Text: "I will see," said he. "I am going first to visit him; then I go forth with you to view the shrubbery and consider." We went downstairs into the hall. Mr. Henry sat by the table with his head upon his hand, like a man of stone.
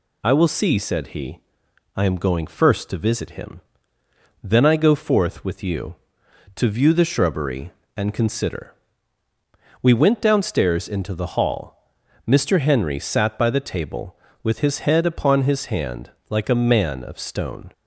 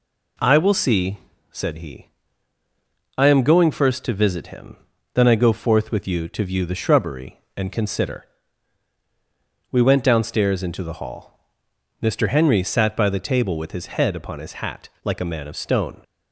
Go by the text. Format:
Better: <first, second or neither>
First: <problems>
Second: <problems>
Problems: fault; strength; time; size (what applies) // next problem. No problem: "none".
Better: first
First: none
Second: says "hat" for "hand"; at 14.6 s